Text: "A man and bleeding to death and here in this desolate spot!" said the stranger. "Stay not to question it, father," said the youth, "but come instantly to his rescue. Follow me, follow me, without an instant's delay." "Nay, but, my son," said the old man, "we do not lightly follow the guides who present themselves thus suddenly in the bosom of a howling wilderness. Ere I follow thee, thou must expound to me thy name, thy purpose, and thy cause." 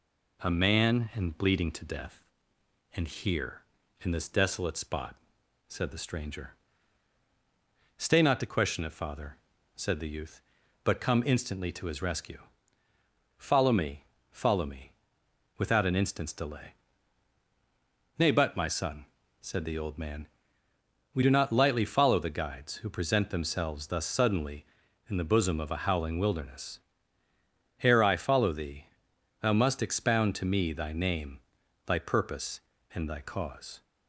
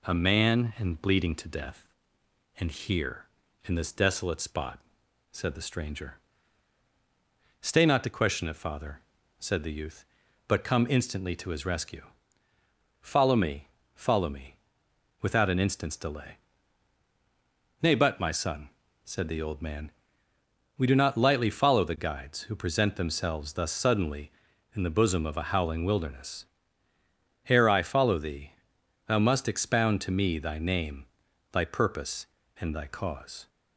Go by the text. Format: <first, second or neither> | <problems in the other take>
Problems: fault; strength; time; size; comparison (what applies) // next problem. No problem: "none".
neither | none